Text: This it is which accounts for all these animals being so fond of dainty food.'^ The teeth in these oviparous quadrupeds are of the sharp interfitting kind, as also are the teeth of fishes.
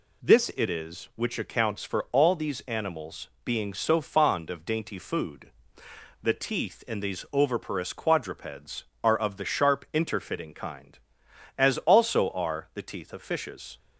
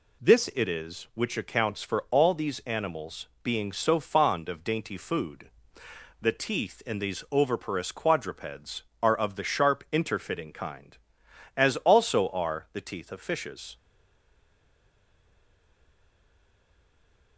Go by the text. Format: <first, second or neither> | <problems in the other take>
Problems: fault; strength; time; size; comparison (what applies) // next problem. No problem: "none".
first | pauses between "animals" and "being"; slight; at 3.2 s; 0.16 s long; slight in the first // stays silent after the last word; strong; from 13.7 s on; 3.6 s long